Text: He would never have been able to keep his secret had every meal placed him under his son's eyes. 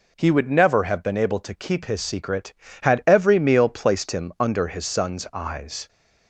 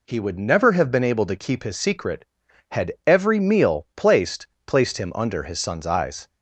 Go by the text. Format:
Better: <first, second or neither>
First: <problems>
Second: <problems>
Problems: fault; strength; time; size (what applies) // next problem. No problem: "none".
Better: first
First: none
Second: says "placed" twice; at 4.6 s